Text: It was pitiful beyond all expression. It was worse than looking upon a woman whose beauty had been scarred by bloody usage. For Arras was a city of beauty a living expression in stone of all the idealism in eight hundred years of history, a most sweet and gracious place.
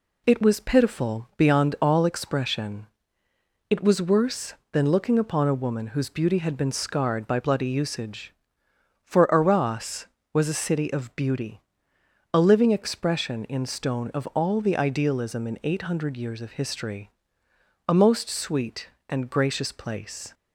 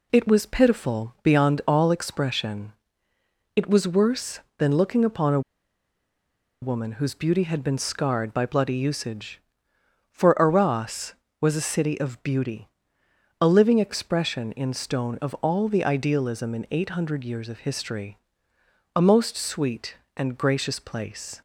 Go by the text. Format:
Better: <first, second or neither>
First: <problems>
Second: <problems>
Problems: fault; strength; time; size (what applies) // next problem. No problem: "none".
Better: first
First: pauses between "beauty" and "a"; noticeable; at 11.5 s; 0.74 s long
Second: pauses between "a" and "woman"; at 5.3 s; 1.2 s long // pauses between "beauty" and "a"; noticeable; at 12.6 s; 0.74 s long